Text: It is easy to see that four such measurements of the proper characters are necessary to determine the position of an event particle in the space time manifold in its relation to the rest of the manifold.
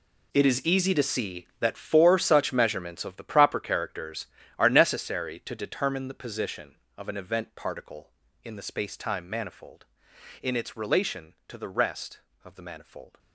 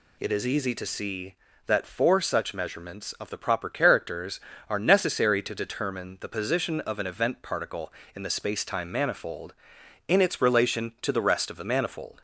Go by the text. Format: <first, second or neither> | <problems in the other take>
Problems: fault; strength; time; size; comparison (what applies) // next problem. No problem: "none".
second | gets quieter; strong; throughout; 14.5 dB